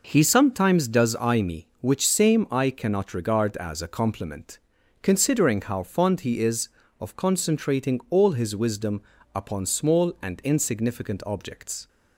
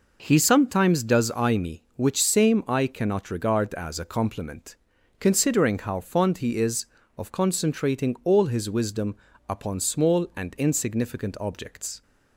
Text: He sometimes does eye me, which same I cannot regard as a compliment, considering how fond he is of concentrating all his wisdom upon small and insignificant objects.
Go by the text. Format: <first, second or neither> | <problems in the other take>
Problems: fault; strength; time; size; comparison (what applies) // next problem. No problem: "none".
neither | pauses between "wisdom" and "upon"; slight; the same in both